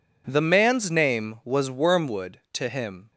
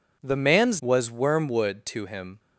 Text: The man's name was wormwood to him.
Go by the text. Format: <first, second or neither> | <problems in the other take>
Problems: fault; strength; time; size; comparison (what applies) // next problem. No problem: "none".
first | skips "name"; at 0.7 s